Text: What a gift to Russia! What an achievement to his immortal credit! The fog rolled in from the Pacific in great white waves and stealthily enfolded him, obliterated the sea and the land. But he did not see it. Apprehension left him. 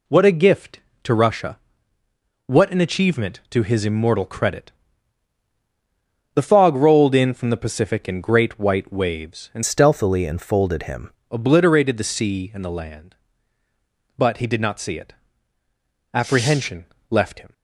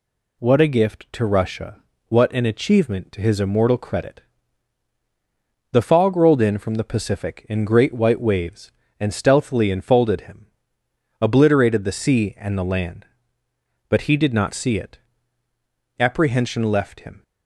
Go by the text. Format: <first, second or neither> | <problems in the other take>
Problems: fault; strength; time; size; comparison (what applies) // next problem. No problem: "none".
second | changes voice from "stealthily" to "him"; from 9.6 to 11.1 s; 1.5 s long // pauses between "Apprehension" and "left"; slight; at 16.8 s; 0.22 s long